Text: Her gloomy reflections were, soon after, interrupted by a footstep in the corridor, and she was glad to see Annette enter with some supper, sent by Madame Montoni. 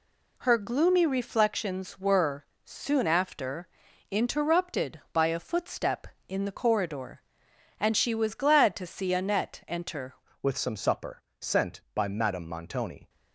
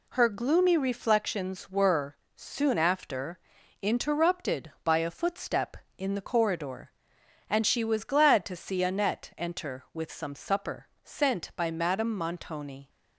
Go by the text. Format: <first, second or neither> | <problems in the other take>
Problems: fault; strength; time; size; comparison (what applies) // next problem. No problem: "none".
second | changes voice at "with"; from 10.4 s on; 2.6 s long